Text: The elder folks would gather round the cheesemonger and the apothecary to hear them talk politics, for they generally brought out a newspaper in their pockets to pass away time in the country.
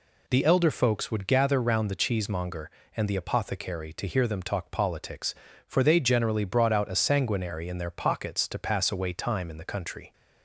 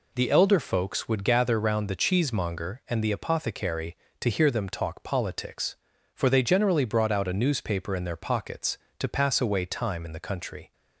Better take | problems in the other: second | says "sanguinary" for "newspaper"; at 6.9 s

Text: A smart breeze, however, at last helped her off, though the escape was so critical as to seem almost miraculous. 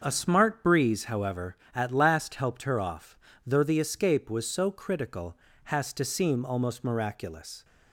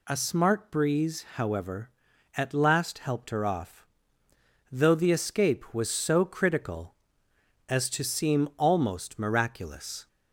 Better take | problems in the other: second | starts louder than the rest; until 1.0 s; 6.5 dB // says "has" for "as"; at 5.6 s

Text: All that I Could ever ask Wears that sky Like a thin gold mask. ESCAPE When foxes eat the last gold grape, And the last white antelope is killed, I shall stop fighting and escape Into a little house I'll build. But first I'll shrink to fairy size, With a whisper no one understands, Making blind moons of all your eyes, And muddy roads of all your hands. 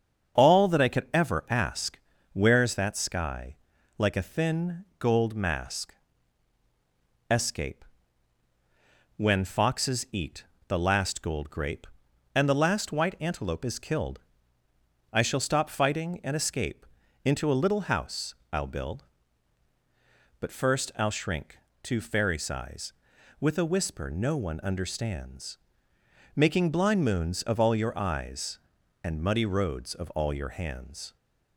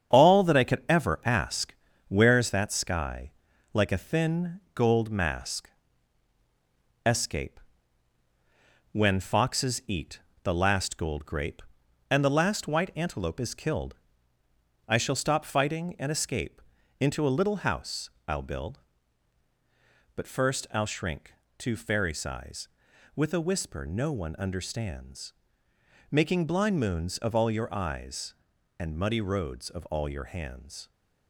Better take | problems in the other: first | gets quieter; throughout; 6.5 dB // starts louder than the rest; strong; until 1.2 s; 8 dB; also in the first // pauses between "ask" and "Wears"; slight; at 1.7 s; 0.36 s long; slight in the first // pauses between "sky" and "Like"; at 3.3 s; 0.40 s long; also in the first // pauses between "ESCAPE" and "When"; strong; at 7.5 s; 1.3 s long; strong in the first // pauses between "eat" and "the"; slight; at 10.1 s; 0.24 s long; slight in the first // pauses between "escape" and "Into"; at 16.5 s; 0.40 s long; also in the first // pauses between "house" and "I'll"; slight; at 18.0 s; 0.18 s long; slight in the first

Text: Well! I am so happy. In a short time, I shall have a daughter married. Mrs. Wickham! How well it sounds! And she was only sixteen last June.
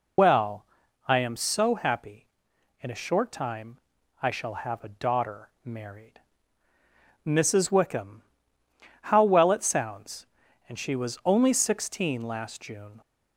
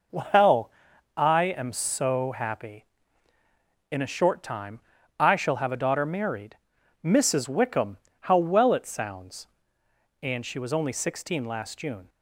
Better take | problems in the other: second | loses the start of "Well"; at 0.1 s; 105 ms

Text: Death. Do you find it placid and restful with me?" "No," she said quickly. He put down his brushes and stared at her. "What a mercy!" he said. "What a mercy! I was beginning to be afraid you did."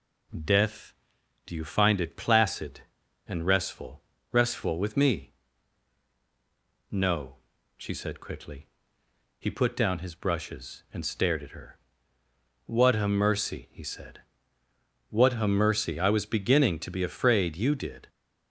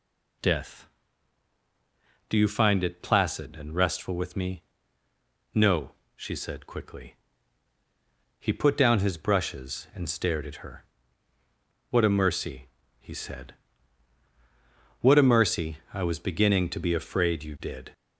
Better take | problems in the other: second | says "restful" twice; at 4.2 s

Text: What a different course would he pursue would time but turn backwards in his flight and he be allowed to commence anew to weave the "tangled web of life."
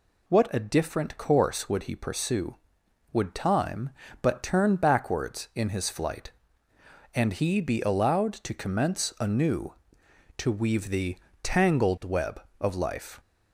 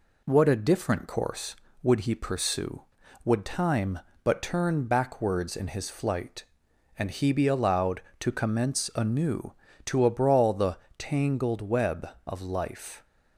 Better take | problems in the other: first | says "abrawl" for "weave"; at 10.0 s // pauses between "the" and "tangled"; slight; at 10.7 s; 0.18 s long; slight in the first

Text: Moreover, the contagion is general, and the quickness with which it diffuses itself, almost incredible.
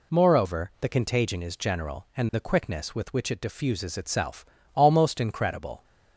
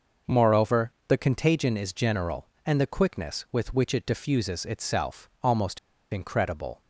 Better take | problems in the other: first | pauses between "almost" and "incredible"; slight; at 5.7 s; 0.35 s long

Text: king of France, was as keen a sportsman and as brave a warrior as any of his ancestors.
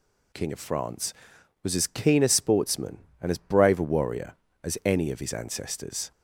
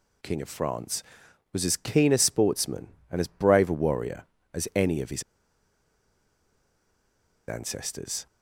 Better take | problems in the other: first | pauses between "his" and "ancestors"; strong; at 5.2 s; 2.2 s long

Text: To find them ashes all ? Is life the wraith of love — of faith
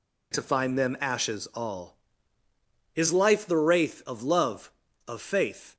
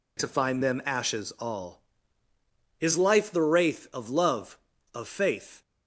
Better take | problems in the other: neither | none

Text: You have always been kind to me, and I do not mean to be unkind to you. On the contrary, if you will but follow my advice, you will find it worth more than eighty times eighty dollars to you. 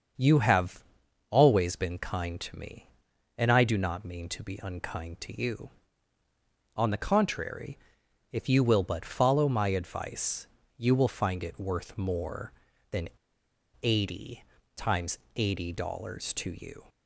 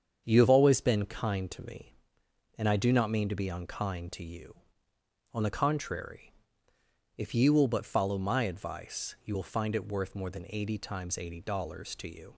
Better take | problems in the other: second | starts louder than the rest; until 1.6 s; 6.5 dB; strong in the second // pauses between "have" and "always"; noticeable; at 0.8 s; 0.46 s long // pauses between "than" and "eighty"; noticeable; at 13.0 s; 0.75 s long // pauses between "eighty" and "times"; slight; at 14.4 s; 0.32 s long // pauses between "times" and "eighty"; slight; at 15.1 s; 0.18 s long

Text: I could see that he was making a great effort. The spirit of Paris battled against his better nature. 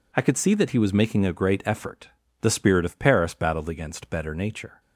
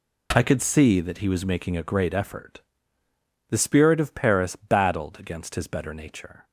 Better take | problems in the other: second | skips "his"; at 4.1 s

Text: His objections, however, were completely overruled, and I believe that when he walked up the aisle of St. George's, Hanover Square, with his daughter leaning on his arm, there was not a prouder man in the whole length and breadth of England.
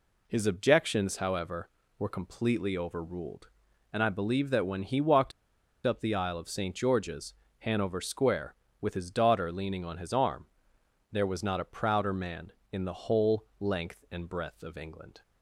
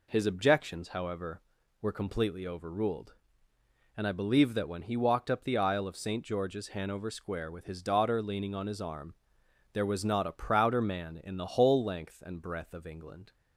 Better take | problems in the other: second | pauses between "walked" and "up"; noticeable; at 5.3 s; 0.53 s long

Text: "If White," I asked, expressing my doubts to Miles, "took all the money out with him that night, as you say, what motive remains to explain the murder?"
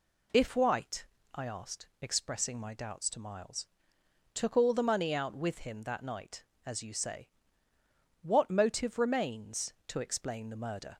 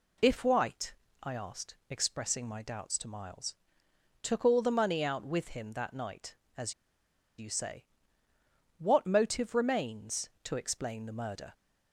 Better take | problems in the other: first | pauses between "as" and "you"; noticeable; at 6.7 s; 0.65 s long

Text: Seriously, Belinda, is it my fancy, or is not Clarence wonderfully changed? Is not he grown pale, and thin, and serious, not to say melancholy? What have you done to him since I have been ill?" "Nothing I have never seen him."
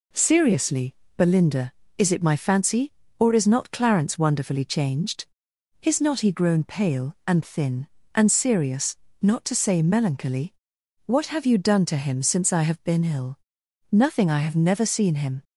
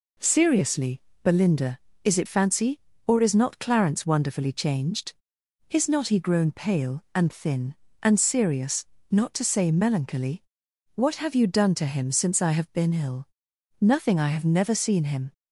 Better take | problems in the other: first | skips "my"; at 2.2 s

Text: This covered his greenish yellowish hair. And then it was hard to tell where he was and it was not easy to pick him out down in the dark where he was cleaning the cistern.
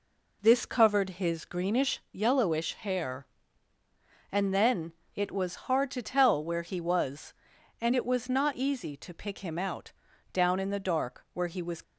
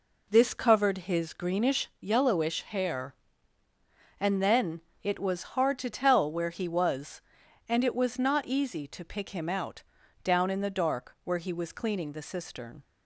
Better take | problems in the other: second | pauses between "then" and "it"; slight; at 4.9 s; 0.24 s long; slight in the second // pauses between "out" and "down"; at 9.9 s; 0.40 s long; also in the second // stops before "cleaning the cistern"; at 11.8 s

